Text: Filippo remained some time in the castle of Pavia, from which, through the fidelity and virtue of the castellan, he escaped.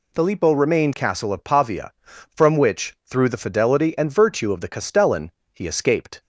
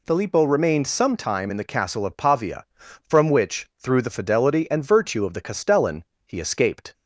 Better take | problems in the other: second | skips "some time in the"; at 0.9 s

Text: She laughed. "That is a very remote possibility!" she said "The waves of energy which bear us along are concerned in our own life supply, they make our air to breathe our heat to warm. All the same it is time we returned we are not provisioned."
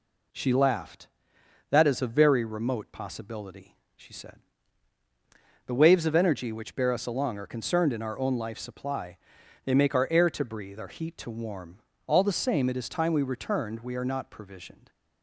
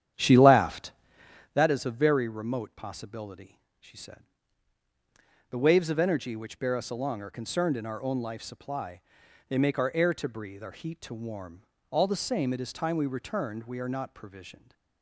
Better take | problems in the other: first | starts louder than the rest; strong; until 1.6 s; 10 dB // pauses between "said" and "The"; strong; at 4.2 s; 1.2 s long; strong in the first

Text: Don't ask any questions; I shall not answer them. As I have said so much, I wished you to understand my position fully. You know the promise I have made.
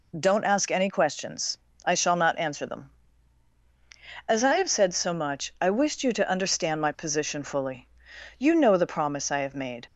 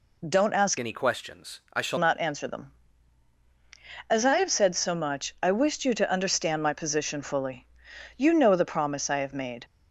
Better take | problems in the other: first | changes voice from "any" to "shall"; from 0.7 to 1.9 s; 1.2 s long

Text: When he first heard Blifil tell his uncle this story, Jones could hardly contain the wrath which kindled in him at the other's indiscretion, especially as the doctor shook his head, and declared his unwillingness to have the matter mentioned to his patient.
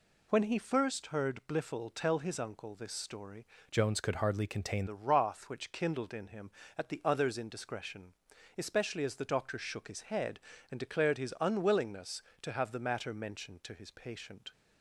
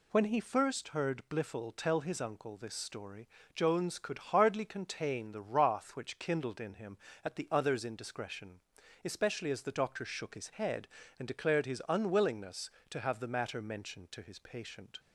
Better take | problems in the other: second | changes voice from "Jones" to "contain"; from 3.7 to 4.8 s; 1.1 s long

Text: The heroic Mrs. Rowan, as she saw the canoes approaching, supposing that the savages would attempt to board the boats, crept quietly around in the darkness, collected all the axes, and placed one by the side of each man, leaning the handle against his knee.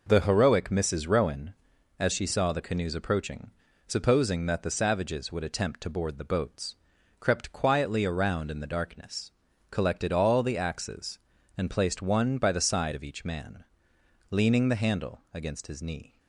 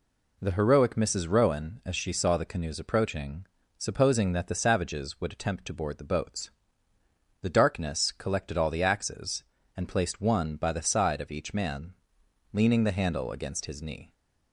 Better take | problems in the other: first | skips "crept quietly around in"; at 6.9 s

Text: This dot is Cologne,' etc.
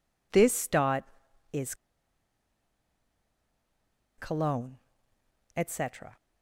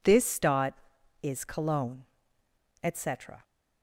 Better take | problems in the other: second | pauses between "is" and "Cologne"; strong; at 1.7 s; 2.4 s long

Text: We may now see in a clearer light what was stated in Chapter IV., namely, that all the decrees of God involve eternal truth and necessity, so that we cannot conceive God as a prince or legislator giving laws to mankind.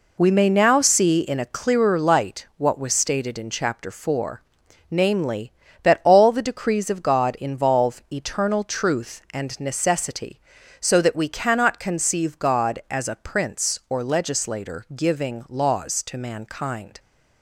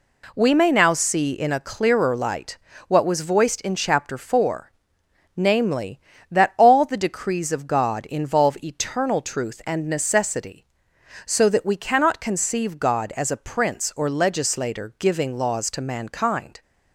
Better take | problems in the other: first | pauses between "light" and "what"; slight; at 2.5 s; 0.32 s long // says "voiced" for "stated"; at 3.2 s

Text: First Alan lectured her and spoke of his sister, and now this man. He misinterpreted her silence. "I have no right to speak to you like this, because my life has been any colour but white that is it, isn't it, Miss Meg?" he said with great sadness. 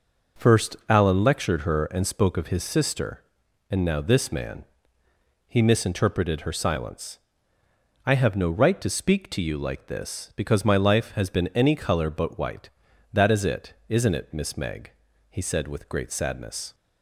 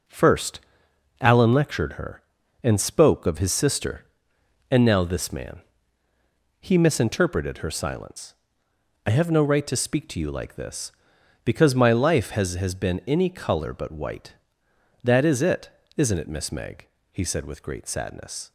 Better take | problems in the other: first | pauses between "First" and "Alan"; noticeable; at 0.5 s; 0.60 s long // says "has" twice; at 12.5 s

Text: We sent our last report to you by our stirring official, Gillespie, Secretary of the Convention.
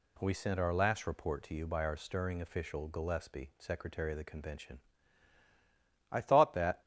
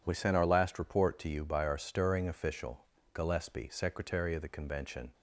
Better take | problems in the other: second | goes on to say "I thought that"; noticeable; from 6.1 s on; 0.70 s long

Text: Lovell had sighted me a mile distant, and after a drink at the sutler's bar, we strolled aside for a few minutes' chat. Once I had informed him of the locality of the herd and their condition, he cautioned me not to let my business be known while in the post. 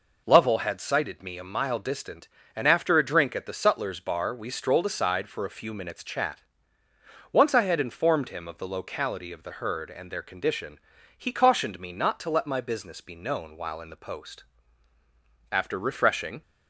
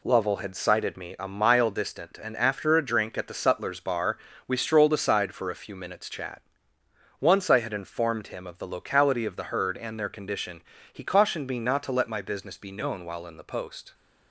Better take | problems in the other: second | goes on to say "After refreshing"; noticeable; from 15.5 s on; 0.90 s long

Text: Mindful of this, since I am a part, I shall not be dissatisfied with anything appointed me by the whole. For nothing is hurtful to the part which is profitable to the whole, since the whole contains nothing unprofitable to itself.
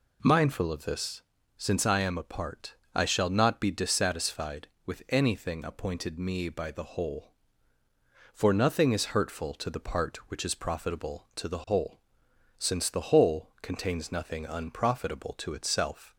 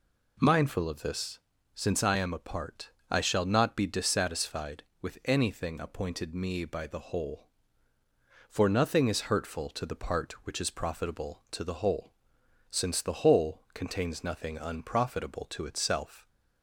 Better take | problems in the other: neither | none

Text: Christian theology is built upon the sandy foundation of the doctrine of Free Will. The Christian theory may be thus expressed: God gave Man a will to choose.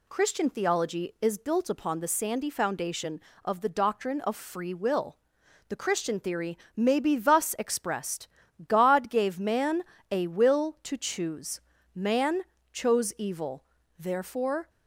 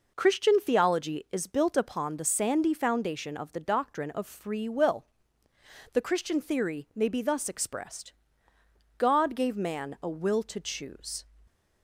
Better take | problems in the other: second | pauses between "theory" and "may"; slight; at 6.5 s; 0.18 s long // pauses between "Man" and "a"; slight; at 9.8 s; 0.26 s long // goes on to say "Man chose evil therefore"; strong; from 11.9 s on; 2.7 s long

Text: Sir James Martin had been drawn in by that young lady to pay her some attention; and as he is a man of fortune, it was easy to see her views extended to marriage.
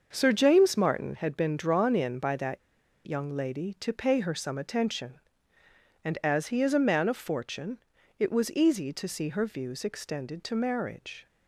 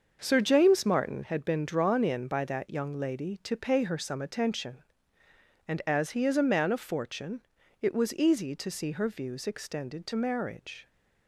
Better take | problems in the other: second | starts louder than the rest; until 1.1 s; 6.5 dB; also in the second // pauses between "that" and "young"; at 2.5 s; 0.45 s long

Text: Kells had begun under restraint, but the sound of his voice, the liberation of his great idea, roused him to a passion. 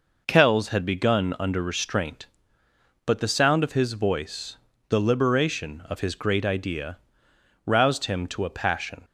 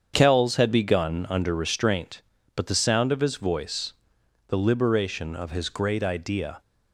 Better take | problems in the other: first | starts louder than the rest; strong; until 1.1 s; 7.5 dB // stops before "roused him to a passion"; at 6.6 s

